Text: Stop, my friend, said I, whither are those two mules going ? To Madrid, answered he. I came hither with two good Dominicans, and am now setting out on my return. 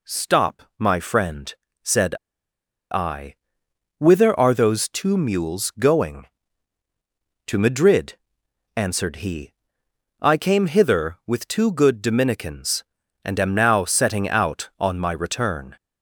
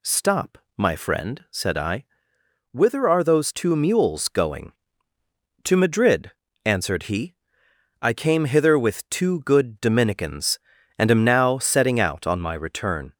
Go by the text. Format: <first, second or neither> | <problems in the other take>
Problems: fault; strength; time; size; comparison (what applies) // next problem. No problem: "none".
second | pauses between "said" and "I"; noticeable; at 2.1 s; 0.77 s long